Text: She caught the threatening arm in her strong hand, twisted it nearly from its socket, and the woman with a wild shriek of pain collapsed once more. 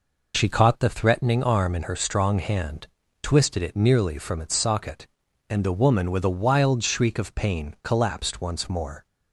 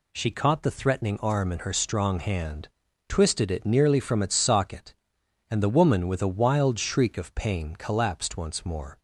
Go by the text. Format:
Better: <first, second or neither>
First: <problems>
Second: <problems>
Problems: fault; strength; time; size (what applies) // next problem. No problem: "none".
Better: neither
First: none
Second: none